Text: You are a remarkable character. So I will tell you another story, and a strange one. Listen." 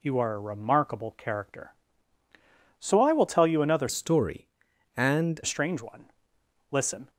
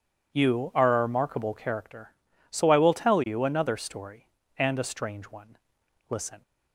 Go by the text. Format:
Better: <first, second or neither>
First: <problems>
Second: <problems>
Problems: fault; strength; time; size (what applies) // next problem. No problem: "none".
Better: second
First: changes voice from "story" to "and"; from 3.8 to 5.3 s; 1.5 s long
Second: none